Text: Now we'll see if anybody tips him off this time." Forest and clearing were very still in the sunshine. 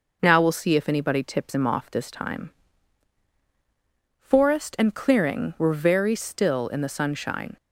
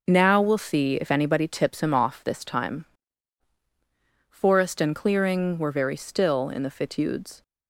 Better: first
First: none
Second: says "fitudes" for "sunshine"; at 6.7 s

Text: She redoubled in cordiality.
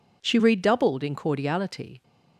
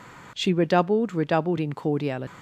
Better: first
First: none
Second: says "redoubled" twice; at 1.1 s

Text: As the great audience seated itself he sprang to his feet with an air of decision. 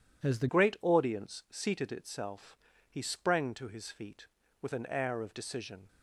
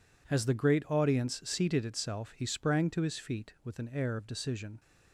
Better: second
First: changes voice at "great"; from 0.4 s on; 5.4 s long // pauses between "itself" and "he"; slight; at 2.5 s; 0.32 s long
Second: none

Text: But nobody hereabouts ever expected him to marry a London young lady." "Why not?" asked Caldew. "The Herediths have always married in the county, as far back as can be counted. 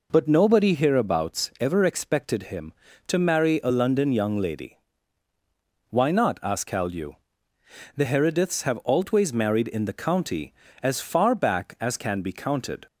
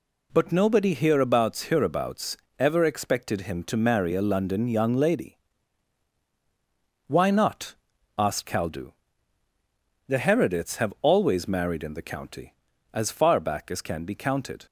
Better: first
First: none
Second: says "hereabouts" twice; at 1.6 s

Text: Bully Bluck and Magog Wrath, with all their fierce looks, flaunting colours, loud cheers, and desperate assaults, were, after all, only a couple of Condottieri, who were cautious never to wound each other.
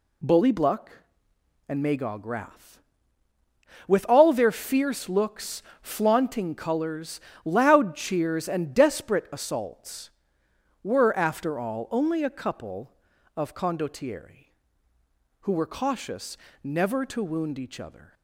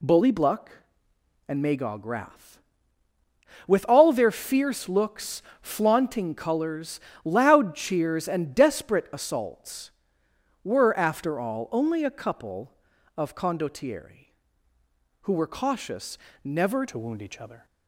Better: first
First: pauses between "cautious" and "never"; slight; at 16.3 s; 0.24 s long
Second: pauses between "cautious" and "never"; slight; at 16.1 s; 0.24 s long // changes voice at "to"; from 16.8 s on; 0.8 s long

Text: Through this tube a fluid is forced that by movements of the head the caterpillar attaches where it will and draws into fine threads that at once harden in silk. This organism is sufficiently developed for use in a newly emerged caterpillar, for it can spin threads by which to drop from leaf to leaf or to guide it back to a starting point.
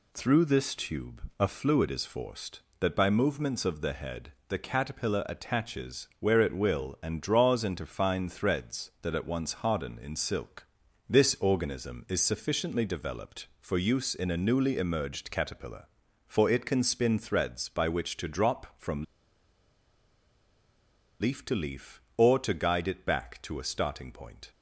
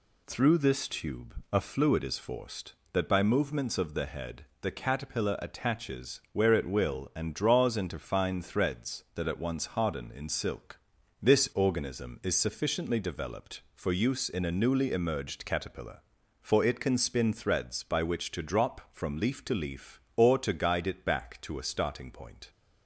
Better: second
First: pauses between "tube" and "a"; slight; at 1.2 s; 0.18 s long // pauses between "head" and "the"; slight; at 4.3 s; 0.16 s long // pauses between "from" and "leaf"; strong; at 19.0 s; 2.1 s long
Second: pauses between "tube" and "a"; slight; at 1.3 s; 0.18 s long // pauses between "head" and "the"; slight; at 4.4 s; 0.16 s long

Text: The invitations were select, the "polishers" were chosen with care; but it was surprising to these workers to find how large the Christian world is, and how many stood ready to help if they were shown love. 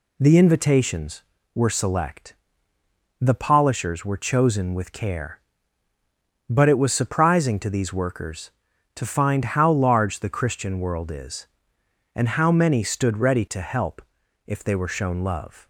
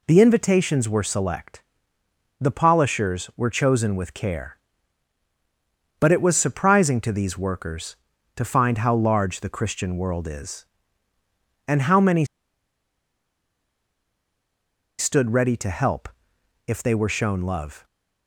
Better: first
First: pauses between "help" and "if"; noticeable; at 13.9 s; 0.46 s long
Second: pauses between "many" and "stood"; strong; at 12.2 s; 2.7 s long // pauses between "help" and "if"; noticeable; at 16.0 s; 0.58 s long

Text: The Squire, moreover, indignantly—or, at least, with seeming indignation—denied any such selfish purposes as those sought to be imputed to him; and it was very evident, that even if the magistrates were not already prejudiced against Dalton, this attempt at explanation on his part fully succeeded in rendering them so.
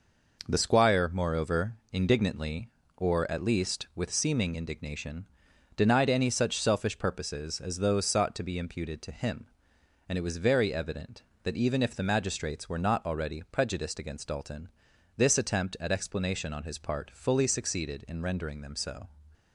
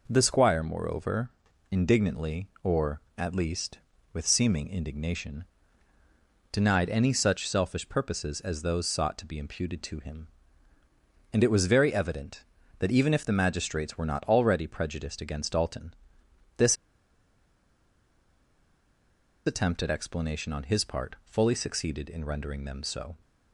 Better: first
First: none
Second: pauses between "this" and "attempt"; strong; at 16.7 s; 2.7 s long

